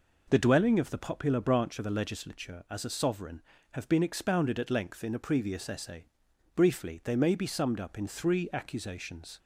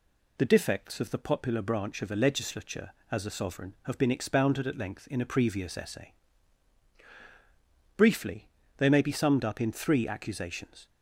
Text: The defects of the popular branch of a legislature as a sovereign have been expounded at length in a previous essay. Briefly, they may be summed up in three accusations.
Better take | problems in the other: second | says "dwelling" for "defects"; at 0.3 s

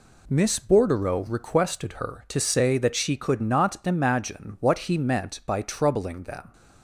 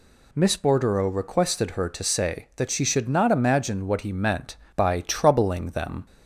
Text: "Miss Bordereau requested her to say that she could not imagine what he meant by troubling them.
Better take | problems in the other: first | says "should" for "could"; at 2.8 s

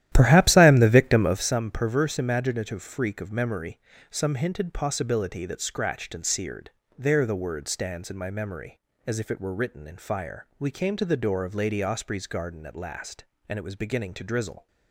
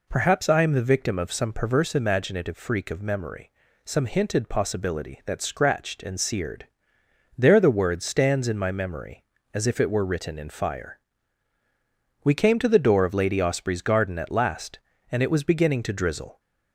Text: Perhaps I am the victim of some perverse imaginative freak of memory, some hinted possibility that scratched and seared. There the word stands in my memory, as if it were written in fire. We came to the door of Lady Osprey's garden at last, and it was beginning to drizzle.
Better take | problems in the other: second | starts louder than the rest; strong; until 1.5 s; 12.5 dB

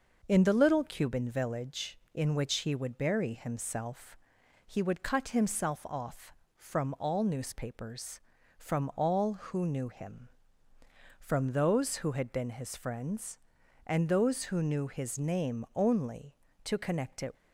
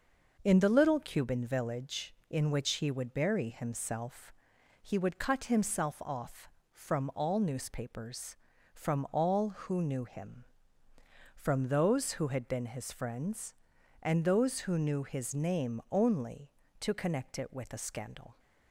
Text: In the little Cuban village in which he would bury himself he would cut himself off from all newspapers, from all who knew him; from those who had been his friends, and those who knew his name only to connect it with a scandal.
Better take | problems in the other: second | pauses between "himself" and "he"; noticeable; at 4.1 s; 0.48 s long; noticeable in the second // stops before "with a scandal"; at 17.3 s

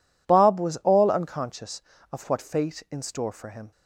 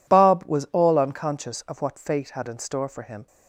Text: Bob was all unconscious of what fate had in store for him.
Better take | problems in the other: second | skips "had"; at 2.8 s

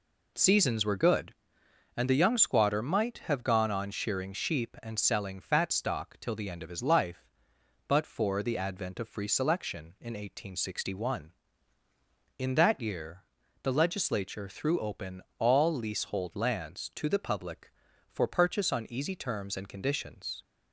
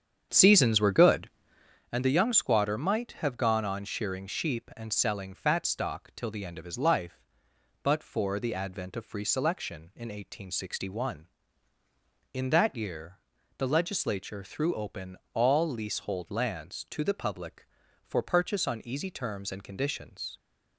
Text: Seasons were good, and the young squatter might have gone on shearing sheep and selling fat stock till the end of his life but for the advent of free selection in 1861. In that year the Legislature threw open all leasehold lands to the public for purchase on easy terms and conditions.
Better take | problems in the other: first | starts louder than the rest; strong; until 1.8 s; 8 dB // pauses between "year" and "the"; at 13.1 s; 0.40 s long; also in the first // pauses between "open" and "all"; slight; at 15.1 s; 0.18 s long; slight in the first

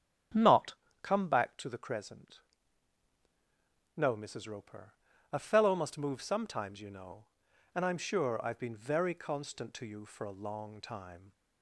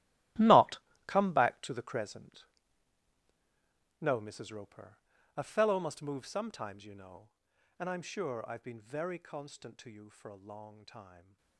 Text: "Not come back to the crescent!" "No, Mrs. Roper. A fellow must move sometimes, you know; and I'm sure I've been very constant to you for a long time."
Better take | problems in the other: first | gets quieter; strong; throughout; 14.5 dB // starts louder than the rest; strong; until 1.6 s; 14 dB; strong in the first // pauses between "Not" and "come"; slight; at 0.7 s; 0.30 s long; slight in the first

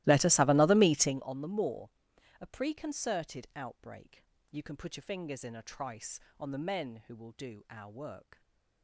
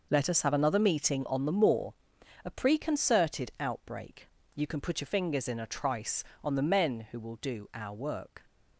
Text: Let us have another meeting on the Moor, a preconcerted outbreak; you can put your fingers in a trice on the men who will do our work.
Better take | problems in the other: second | starts louder than the rest; strong; until 1.3 s; 17 dB // stays silent after the last word; slight; from 8.3 s on; 0.5 s long

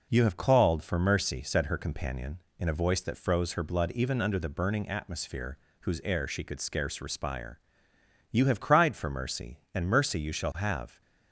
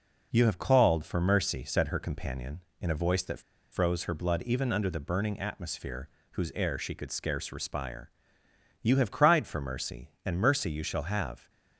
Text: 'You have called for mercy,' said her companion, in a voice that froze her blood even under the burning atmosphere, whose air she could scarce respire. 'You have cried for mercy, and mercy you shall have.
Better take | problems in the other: first | pauses between "that" and "froze"; slight; at 3.4 s; 0.31 s long

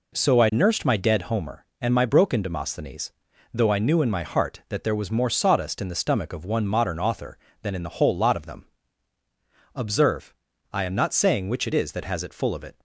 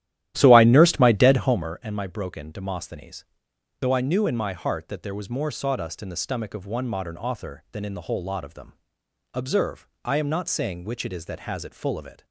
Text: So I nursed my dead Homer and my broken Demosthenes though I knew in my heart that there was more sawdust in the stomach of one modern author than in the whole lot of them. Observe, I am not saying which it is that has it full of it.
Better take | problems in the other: first | starts louder than the rest; strong; until 1.8 s; 13 dB // pauses between "Demosthenes" and "though"; noticeable; at 3.2 s; 0.58 s long; also in the first

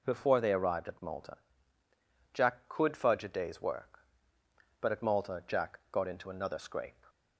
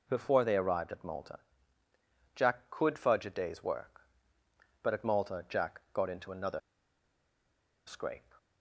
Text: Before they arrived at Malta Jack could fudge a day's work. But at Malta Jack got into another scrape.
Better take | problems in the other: first | pauses between "Malta" and "Jack"; noticeable; at 1.3 s; 0.96 s long; noticeable in the first // pauses between "another" and "scrape"; strong; at 6.6 s; 1.2 s long

